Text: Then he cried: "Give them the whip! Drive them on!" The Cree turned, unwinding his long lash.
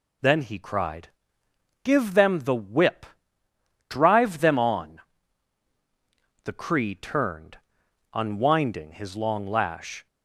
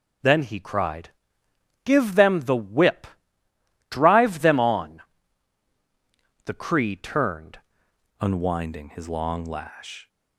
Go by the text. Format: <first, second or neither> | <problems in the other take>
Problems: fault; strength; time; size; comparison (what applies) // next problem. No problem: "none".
first | starts louder than the rest; until 1.9 s; 6.5 dB // changes voice at "unwinding"; from 8.2 s on; 1.8 s long